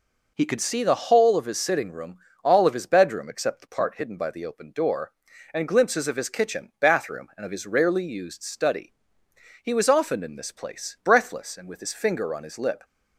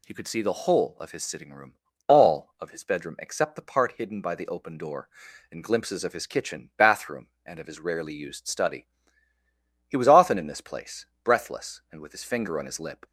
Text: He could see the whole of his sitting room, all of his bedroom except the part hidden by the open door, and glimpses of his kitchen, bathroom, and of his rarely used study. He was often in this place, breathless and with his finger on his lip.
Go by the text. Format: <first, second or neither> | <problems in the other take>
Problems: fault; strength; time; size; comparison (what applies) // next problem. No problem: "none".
second | starts louder than the rest; noticeable; until 1.3 s; 4.5 dB